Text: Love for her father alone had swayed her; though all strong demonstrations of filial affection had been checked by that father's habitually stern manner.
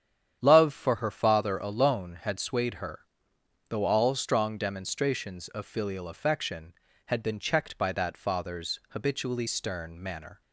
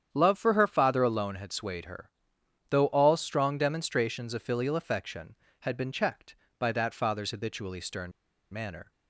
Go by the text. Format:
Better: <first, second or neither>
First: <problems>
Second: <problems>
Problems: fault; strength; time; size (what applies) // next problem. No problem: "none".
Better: first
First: starts louder than the rest; strong; until 1.4 s; 9 dB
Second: starts louder than the rest; strong; until 1.1 s; 9 dB // pauses between "stern" and "manner"; at 8.1 s; 0.40 s long